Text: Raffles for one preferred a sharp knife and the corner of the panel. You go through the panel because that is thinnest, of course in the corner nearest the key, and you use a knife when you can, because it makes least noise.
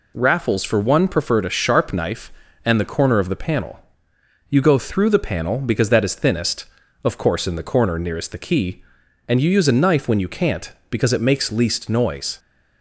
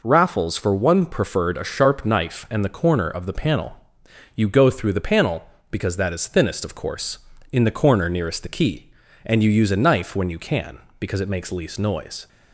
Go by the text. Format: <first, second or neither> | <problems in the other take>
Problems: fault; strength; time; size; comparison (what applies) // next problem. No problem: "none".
second | says "can't" for "can"; at 10.2 s